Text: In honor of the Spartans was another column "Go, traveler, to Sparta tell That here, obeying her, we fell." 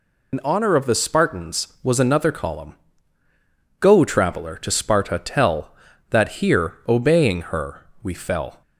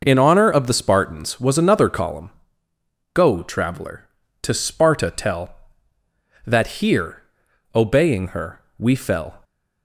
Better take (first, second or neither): second